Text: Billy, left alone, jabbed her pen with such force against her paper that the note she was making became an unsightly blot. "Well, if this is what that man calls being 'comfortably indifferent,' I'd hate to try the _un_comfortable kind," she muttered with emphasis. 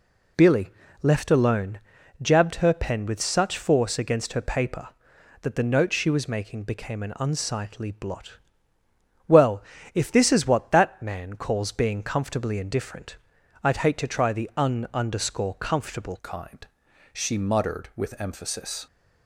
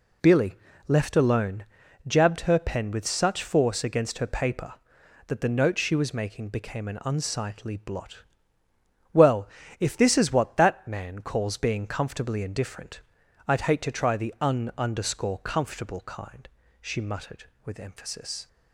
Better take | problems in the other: second | changes voice at "kind"; from 16.2 s on; 2.6 s long

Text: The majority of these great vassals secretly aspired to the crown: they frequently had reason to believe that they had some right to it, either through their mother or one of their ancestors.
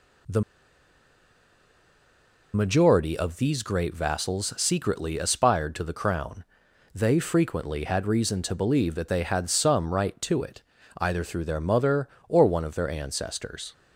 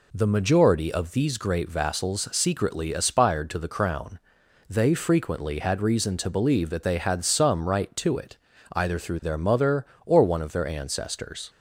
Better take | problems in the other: second | pauses between "The" and "majority"; strong; at 0.4 s; 2.1 s long

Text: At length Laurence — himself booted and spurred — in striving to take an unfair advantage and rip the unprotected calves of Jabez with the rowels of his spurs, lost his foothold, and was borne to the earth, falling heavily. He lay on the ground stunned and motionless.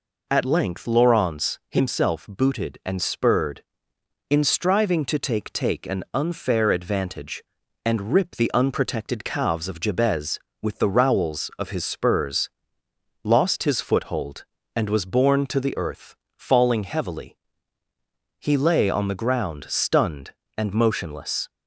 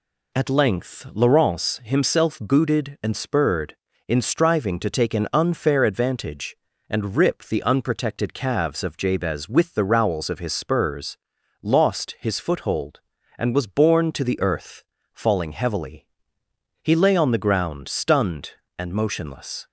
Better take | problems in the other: second | says "take" twice; at 5.5 s

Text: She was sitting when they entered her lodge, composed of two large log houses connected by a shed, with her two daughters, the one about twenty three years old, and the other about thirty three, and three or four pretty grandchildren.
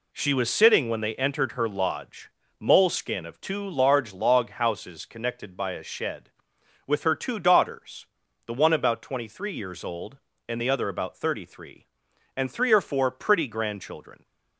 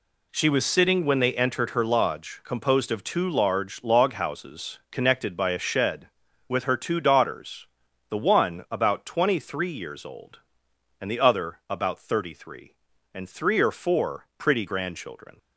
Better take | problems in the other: second | says "moleskin" for "composed"; at 2.6 s

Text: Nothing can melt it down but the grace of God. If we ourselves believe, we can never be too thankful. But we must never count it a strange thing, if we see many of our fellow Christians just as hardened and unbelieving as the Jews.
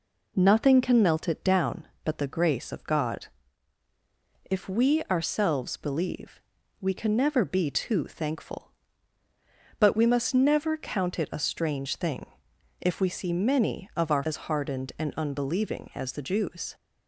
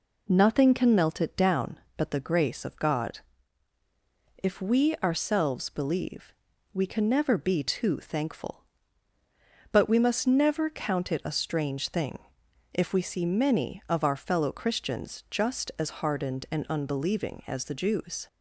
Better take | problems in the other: second | skips "fellow Christians just"; at 14.2 s

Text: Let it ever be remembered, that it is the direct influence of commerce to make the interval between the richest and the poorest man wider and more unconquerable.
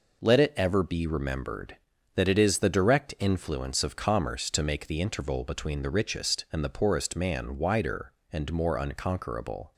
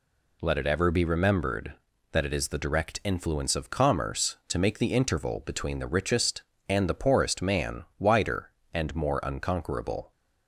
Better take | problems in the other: neither | none

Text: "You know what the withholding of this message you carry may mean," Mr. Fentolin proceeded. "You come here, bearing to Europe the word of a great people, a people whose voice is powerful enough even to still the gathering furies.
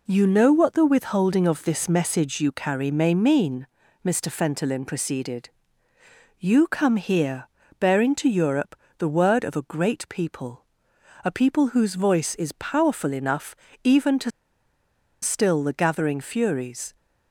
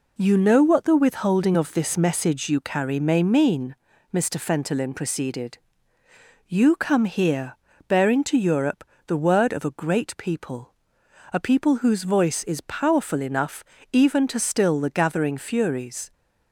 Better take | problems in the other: second | pauses between "Europe" and "the"; slight; at 8.7 s; 0.24 s long; slight in the second // pauses between "enough" and "even"; slight; at 13.5 s; 0.28 s long; slight in the second // pauses between "to" and "still"; noticeable; at 14.2 s; 0.92 s long

